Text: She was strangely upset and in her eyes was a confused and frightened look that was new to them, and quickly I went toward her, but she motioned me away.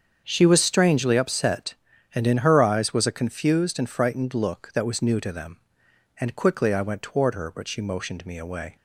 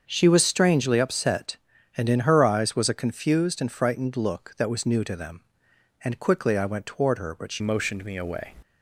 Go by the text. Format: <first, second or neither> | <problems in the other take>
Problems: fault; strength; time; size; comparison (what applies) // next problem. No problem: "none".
first | starts louder than the rest; until 1.0 s; 7 dB; strong in the first // changes voice at "motioned"; from 7.5 s on; 1.0 s long